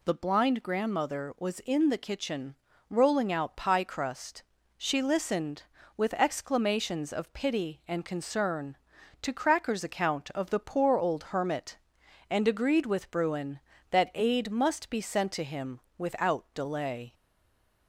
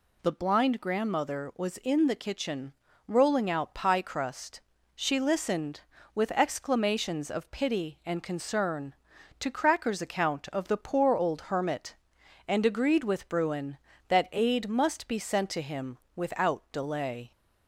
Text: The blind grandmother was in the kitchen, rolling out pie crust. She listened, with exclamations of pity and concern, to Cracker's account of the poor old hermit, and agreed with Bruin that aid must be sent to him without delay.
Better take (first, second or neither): second